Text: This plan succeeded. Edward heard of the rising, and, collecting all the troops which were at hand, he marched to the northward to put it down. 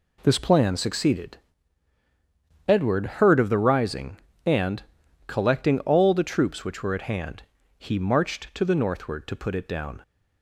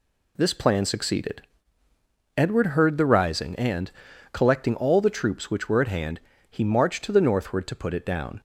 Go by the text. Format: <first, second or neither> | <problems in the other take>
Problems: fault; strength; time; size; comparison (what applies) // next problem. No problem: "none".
first | skips "of"; at 2.9 s